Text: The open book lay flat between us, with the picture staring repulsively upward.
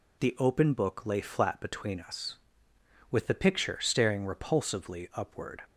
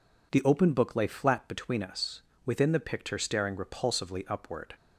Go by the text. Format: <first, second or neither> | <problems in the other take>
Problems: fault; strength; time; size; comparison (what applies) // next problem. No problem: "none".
first | says "within" for "with"; at 2.4 s